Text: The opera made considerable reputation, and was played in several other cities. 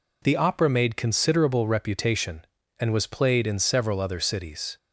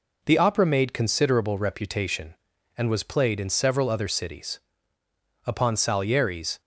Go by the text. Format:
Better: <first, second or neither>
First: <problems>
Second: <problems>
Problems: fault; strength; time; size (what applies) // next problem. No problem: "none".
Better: first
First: none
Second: goes on to say "Upon Salieri's"; noticeable; from 5.4 s on; 1.1 s long